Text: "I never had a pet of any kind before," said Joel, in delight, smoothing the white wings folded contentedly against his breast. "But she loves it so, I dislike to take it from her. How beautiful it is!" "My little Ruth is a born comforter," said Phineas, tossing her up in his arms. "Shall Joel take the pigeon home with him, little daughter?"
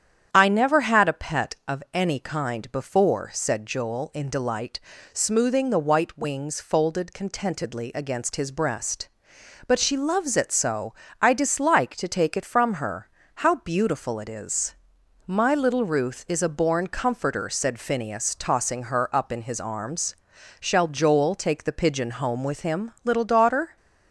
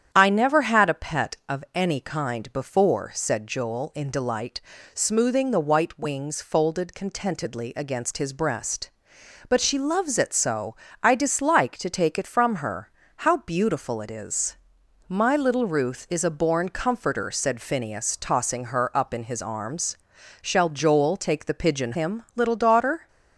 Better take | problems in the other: first | starts louder than the rest; strong; until 1.1 s; 9.5 dB; strong in the first // skips "home with"; at 21.9 s

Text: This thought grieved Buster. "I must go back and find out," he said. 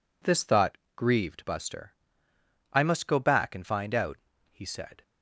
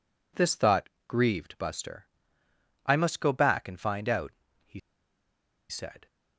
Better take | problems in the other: first | pauses between "thought" and "grieved"; slight; at 0.8 s; 0.18 s long; slight in the first // pauses between "he" and "said"; noticeable; at 4.7 s; 0.90 s long

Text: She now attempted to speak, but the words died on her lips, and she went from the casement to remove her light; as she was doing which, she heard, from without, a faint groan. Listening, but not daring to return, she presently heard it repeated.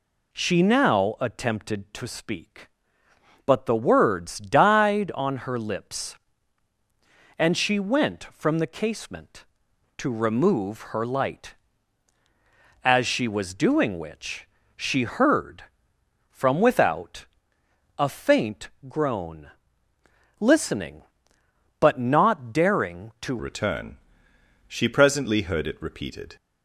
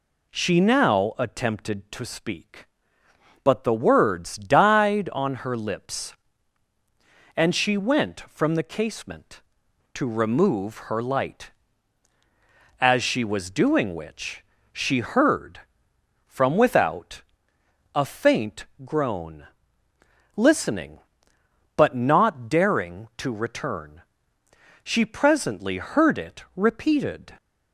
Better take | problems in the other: second | pauses between "faint" and "groan"; slight; at 18.6 s; 0.18 s long; slight in the second // changes voice at "return"; from 23.3 s on; 3.0 s long

